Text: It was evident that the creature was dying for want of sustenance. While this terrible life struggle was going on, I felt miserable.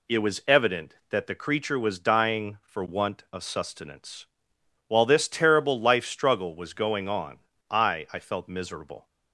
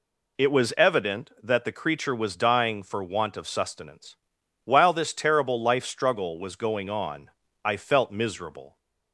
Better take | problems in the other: second | says "I" twice; at 8.1 s

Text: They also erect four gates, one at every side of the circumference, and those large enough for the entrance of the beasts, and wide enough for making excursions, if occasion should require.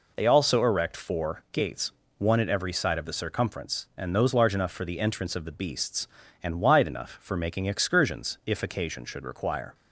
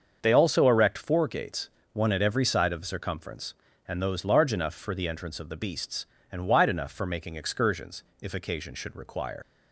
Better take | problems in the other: first | starts louder than the rest; until 1.2 s; 7 dB // leaves "require" unfinished; at 9.4 s; 120 ms

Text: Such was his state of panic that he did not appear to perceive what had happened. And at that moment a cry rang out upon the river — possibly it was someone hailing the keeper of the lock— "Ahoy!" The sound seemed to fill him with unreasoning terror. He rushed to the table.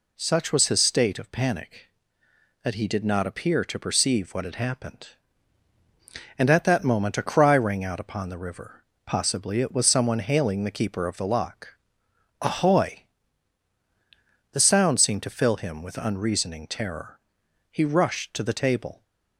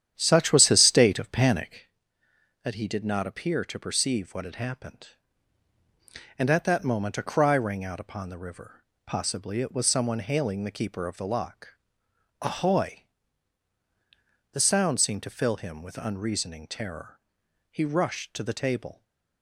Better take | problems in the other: first | starts louder than the rest; strong; until 1.8 s; 10 dB

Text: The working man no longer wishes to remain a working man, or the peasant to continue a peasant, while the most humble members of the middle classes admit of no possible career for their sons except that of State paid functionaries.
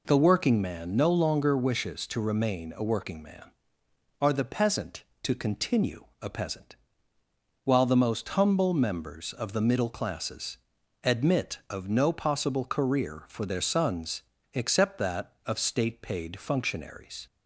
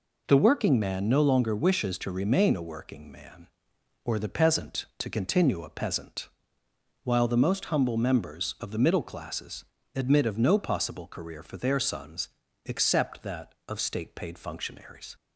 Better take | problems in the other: second | says "are" for "or"; at 4.2 s // pauses between "continue" and "a"; slight; at 6.0 s; 0.18 s long // pauses between "classes" and "admit"; at 10.5 s; 0.44 s long; slight in the second // pauses between "sons" and "except"; slight; at 14.2 s; 0.32 s long; slight in the second

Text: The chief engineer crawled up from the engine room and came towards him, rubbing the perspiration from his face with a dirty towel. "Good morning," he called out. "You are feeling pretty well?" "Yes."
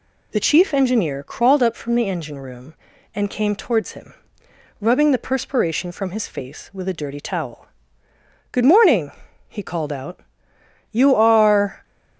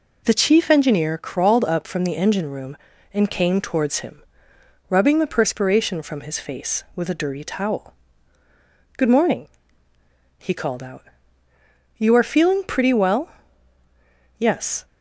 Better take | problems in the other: second | stops before "feeling pretty well Yes"; at 11.8 s

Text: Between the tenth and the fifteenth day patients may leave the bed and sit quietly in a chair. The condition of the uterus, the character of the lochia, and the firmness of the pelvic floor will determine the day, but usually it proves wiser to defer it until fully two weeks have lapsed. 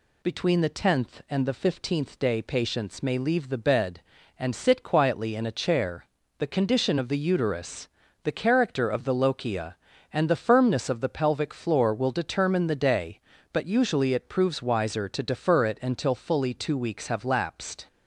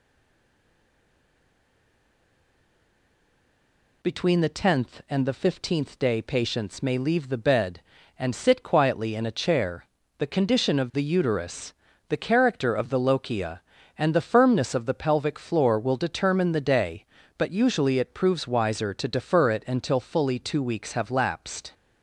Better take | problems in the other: first | stays silent before the first word; strong; until 4.0 s; 4.0 s long

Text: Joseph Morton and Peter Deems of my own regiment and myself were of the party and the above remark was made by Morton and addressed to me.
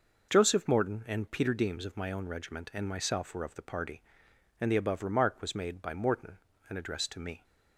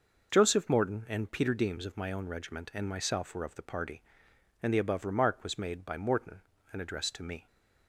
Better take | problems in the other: neither | none

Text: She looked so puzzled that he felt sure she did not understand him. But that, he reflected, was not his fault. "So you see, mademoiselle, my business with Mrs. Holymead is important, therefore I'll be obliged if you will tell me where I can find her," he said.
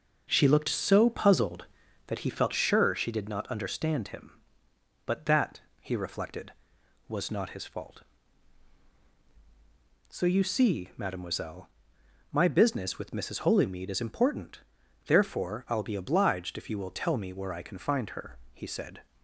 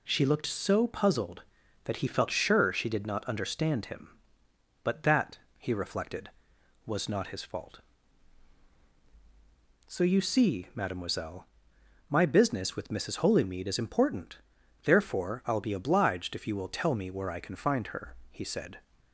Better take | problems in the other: second | starts louder than the rest; noticeable; until 2.1 s; 6 dB

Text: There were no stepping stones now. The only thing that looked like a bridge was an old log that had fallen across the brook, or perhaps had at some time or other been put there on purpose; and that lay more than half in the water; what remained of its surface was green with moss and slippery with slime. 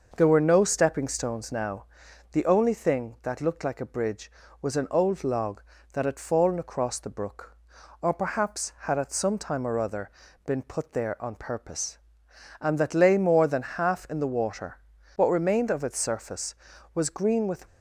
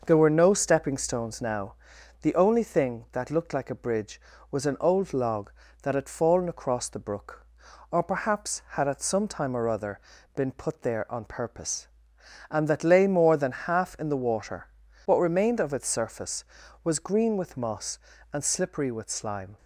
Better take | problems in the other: second | pauses between "other" and "been"; slight; at 10.0 s; 0.36 s long; slight in the second // stops before "moss and slippery with slime"; at 17.6 s

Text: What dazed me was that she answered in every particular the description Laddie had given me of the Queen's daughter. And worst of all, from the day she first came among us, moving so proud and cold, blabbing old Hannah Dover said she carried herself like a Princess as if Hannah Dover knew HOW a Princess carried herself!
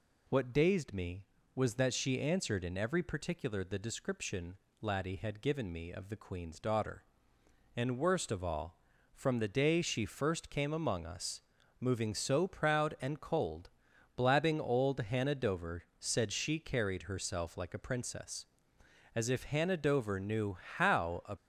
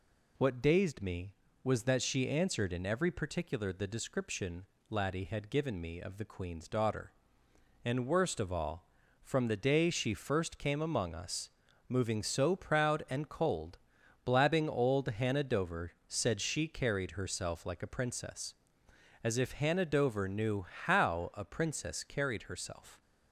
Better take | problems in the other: second | pauses between "description" and "Laddie"; slight; at 4.5 s; 0.26 s long; slight in the second // pauses between "knew" and "HOW"; slight; at 20.5 s; 0.20 s long; slight in the second // stops before "Princess carried herself"; at 21.3 s

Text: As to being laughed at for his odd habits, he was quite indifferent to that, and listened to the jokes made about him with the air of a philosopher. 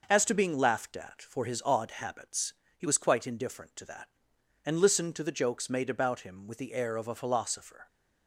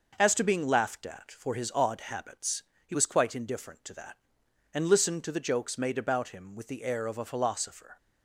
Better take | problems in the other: neither | none

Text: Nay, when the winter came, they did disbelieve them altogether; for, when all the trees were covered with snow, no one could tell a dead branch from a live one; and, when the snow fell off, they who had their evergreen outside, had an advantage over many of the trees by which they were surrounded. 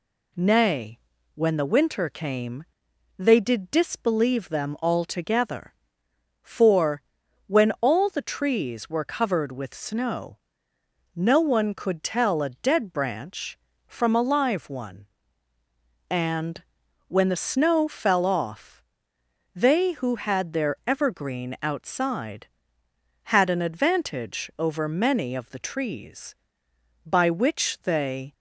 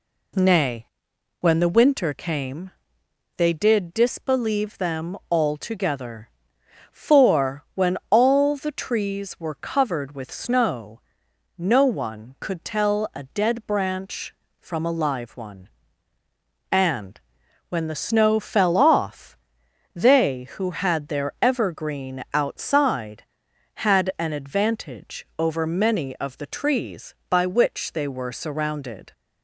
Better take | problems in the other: second | stops before "were surrounded"; at 28.3 s

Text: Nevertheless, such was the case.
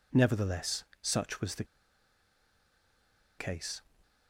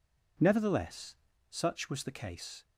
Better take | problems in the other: second | pauses between "the" and "case"; strong; at 1.6 s; 1.7 s long

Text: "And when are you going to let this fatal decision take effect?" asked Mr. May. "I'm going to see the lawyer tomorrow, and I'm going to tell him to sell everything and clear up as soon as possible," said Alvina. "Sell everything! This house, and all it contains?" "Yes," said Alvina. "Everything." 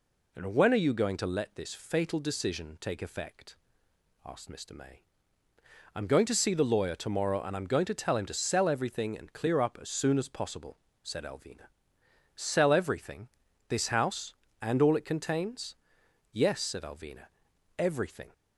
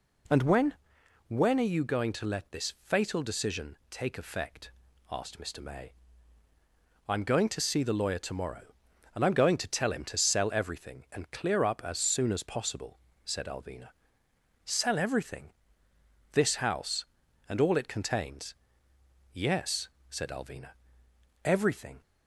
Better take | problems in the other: first | says "when" twice; at 1.2 s

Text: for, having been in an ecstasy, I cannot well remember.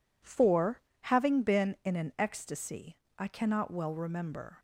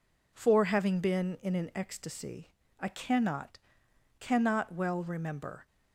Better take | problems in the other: first | says "cannot" twice; at 4.2 s

